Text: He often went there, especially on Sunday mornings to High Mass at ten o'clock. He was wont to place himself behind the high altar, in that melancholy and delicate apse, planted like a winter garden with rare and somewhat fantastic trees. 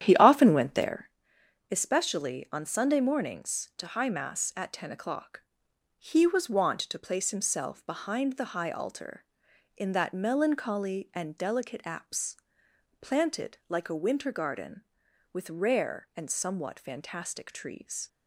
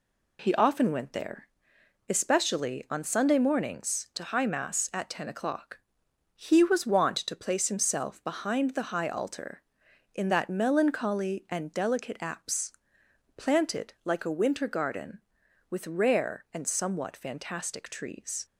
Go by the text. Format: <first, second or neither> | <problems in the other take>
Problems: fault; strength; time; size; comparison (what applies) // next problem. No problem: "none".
second | starts louder than the rest; strong; until 1.1 s; 10.5 dB